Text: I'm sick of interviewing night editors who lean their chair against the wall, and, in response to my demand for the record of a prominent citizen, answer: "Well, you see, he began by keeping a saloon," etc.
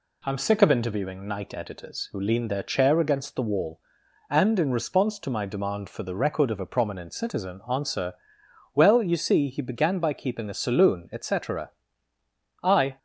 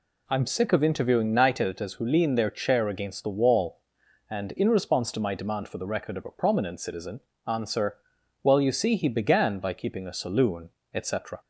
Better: second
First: goes on to say "I"; slight; from 12.6 s on; 0.36 s long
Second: none

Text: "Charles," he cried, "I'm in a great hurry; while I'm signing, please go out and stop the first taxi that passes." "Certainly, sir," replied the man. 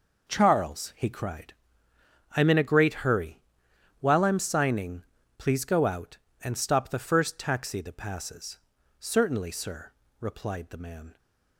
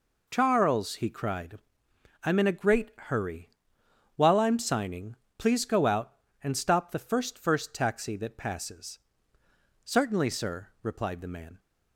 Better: first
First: none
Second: says "first" twice; at 7.3 s

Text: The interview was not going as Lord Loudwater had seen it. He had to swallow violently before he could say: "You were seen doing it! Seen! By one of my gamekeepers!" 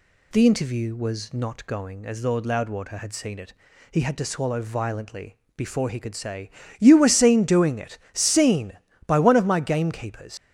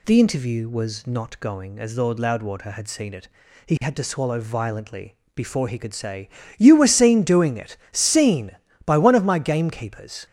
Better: second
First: pauses between "violently" and "before"; slight; at 5.3 s; 0.22 s long // leaves "gamekeepers" unfinished; at 10.3 s; 90 ms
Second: pauses between "violently" and "before"; slight; at 5.1 s; 0.22 s long

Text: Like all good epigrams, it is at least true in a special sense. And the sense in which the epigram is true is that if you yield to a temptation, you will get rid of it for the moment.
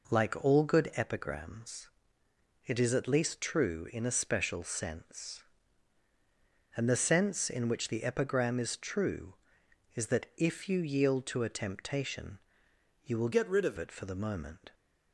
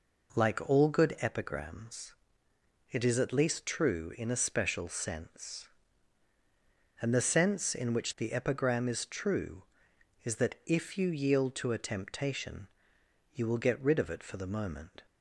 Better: second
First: changes voice from "get" to "of"; from 13.3 to 13.7 s; 0.4 s long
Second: none

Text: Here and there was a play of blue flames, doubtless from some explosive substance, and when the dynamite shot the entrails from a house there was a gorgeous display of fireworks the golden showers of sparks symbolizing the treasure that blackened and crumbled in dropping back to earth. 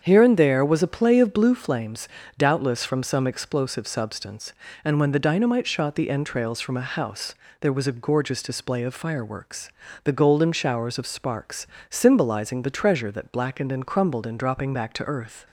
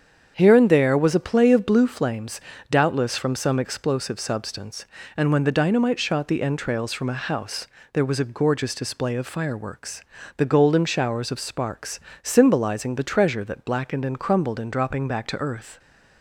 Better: neither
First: starts louder than the rest; strong; until 1.0 s; 7.5 dB // pauses between "house" and "there"; slight; at 7.3 s; 0.24 s long // pauses between "fireworks" and "the"; slight; at 9.6 s; 0.33 s long // pauses between "sparks" and "symbolizing"; slight; at 11.6 s; 0.24 s long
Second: starts louder than the rest; strong; until 1.3 s; 7.5 dB // pauses between "house" and "there"; slight; at 7.6 s; 0.24 s long // pauses between "fireworks" and "the"; slight; at 10.0 s; 0.34 s long // pauses between "sparks" and "symbolizing"; slight; at 12.0 s; 0.24 s long

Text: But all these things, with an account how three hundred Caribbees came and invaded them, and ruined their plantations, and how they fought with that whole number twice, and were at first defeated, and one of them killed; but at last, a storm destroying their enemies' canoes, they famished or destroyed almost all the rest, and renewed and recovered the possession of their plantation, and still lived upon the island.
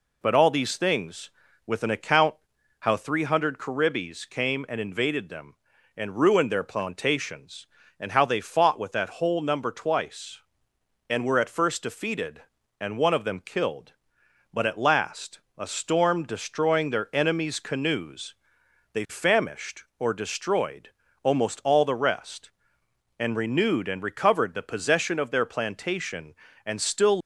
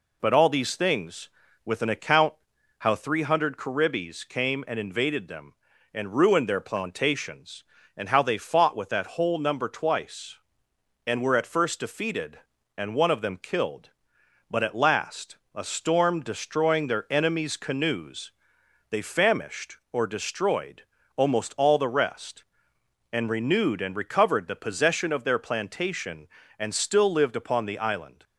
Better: second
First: pauses between "account" and "how"; at 2.3 s; 0.44 s long // pauses between "destroyed" and "almost"; slight; at 20.9 s; 0.34 s long // stops before "lived upon the island"; at 27.2 s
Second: pauses between "account" and "how"; at 2.3 s; 0.44 s long // pauses between "destroyed" and "almost"; slight; at 20.8 s; 0.34 s long

